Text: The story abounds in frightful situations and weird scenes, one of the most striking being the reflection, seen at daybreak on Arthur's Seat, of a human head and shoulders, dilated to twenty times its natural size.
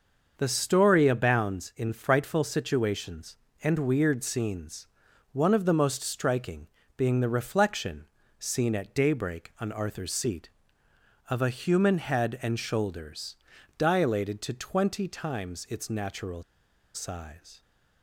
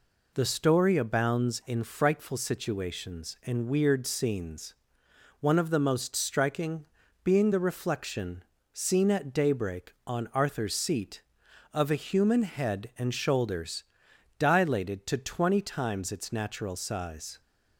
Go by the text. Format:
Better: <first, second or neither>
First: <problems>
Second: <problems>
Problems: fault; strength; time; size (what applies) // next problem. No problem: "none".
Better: second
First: starts louder than the rest; until 1.3 s; 6 dB // pauses between "striking" and "being"; slight; at 6.6 s; 0.32 s long // pauses between "natural" and "size"; noticeable; at 16.4 s; 0.52 s long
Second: pauses between "striking" and "being"; slight; at 6.8 s; 0.36 s long